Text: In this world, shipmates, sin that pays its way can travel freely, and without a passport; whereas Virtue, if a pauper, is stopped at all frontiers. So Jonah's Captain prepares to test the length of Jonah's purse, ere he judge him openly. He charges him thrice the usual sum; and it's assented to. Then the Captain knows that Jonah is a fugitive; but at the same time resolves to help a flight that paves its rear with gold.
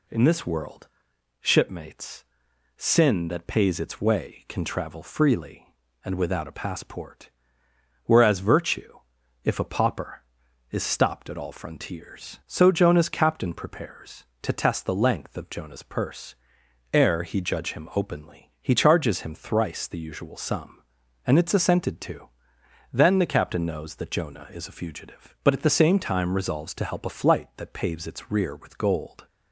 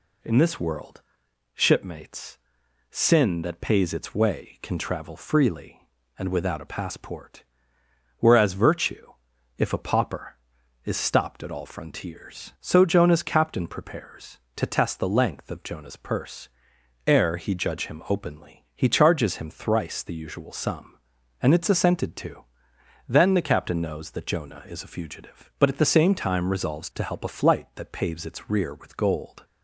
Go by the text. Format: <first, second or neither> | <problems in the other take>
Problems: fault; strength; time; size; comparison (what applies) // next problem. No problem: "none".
neither | none